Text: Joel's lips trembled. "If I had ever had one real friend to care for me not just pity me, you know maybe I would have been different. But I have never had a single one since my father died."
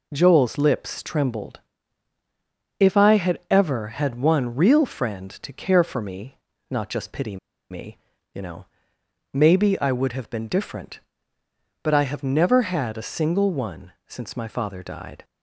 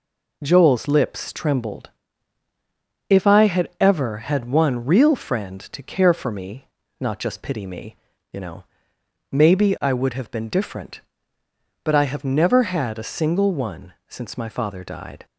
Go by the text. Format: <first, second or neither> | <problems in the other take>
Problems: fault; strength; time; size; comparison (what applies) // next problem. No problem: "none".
second | pauses between "me" and "not"; slight; at 6.3 s; 0.32 s long; slight in the second // pauses between "pity" and "me"; slight; at 7.3 s; 0.33 s long // pauses between "know" and "maybe"; noticeable; at 8.6 s; 0.70 s long; noticeable in the second // pauses between "one" and "since"; slight; at 13.9 s; 0.16 s long; slight in the second